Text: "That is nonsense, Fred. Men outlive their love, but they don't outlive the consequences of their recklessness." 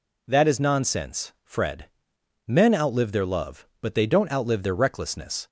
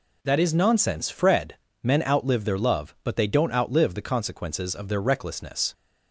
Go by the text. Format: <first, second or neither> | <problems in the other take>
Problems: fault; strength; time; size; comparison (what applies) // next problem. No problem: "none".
second | skips "the consequences of"; at 4.6 s